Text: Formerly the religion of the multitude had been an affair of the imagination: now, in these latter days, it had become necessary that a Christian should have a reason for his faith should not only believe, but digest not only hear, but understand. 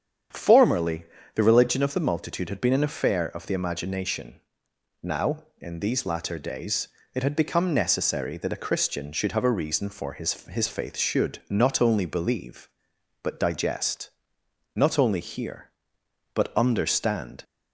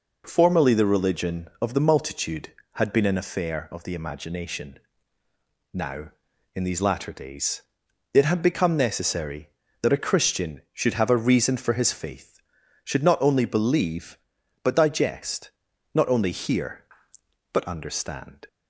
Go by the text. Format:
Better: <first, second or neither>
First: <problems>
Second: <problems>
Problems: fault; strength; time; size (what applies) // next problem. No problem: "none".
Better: second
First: starts louder than the rest; strong; until 1.6 s; 8.5 dB // pauses between "Formerly" and "the"; slight; at 1.0 s; 0.30 s long // says "his" twice; at 10.4 s // pauses between "digest" and "not"; noticeable; at 14.0 s; 0.64 s long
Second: pauses between "digest" and "not"; at 15.5 s; 0.42 s long